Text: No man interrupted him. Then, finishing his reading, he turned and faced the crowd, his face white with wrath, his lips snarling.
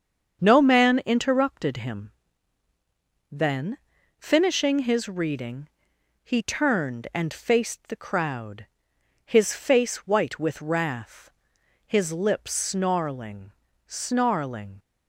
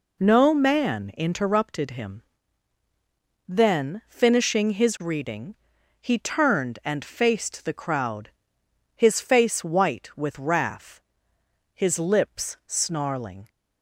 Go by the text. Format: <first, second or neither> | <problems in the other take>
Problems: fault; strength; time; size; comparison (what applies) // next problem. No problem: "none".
second | starts louder than the rest; strong; until 1.4 s; 7 dB // says "snarling" twice; at 13.9 s